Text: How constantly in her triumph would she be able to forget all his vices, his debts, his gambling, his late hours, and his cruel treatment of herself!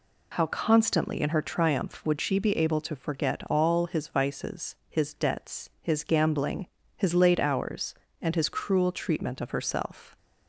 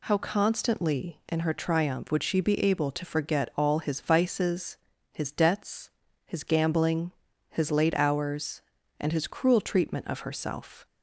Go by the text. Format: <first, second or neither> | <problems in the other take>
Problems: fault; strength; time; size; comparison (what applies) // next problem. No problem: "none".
neither | none